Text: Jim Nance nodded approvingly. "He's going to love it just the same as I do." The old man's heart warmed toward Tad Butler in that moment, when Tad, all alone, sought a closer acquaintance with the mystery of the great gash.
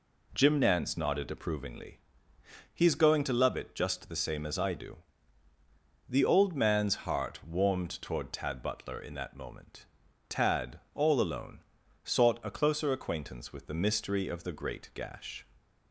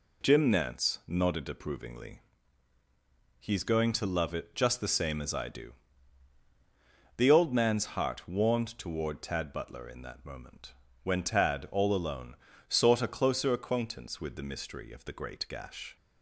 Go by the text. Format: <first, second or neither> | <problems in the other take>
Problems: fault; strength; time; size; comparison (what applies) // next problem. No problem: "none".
second | skips "when"; at 10.0 s